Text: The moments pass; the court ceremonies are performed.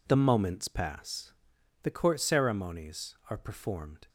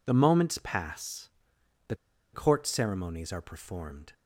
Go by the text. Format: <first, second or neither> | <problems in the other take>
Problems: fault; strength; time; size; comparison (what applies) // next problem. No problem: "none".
first | pauses between "the" and "court"; at 1.9 s; 0.38 s long